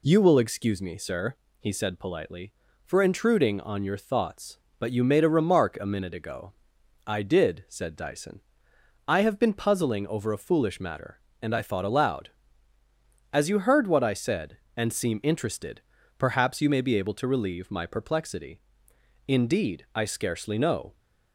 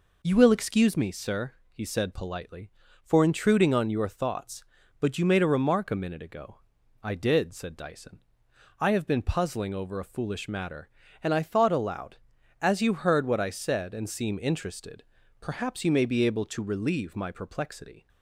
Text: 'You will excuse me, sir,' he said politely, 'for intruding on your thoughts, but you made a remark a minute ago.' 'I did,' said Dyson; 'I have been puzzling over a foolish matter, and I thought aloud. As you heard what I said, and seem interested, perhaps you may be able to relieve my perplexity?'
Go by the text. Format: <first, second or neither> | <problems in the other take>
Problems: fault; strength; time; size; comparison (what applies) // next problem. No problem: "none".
second | goes on to say "Indeed I scarcely know"; strong; from 19.2 s on; 1.7 s long